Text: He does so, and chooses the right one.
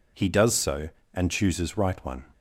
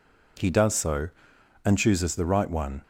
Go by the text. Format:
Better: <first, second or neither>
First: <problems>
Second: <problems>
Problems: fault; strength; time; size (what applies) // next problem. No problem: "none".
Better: second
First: skips "the"; at 1.7 s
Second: none